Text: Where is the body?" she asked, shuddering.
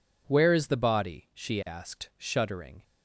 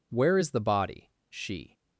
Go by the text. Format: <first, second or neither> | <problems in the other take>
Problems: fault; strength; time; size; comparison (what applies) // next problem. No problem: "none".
first | stops before "asked shuddering"; at 1.7 s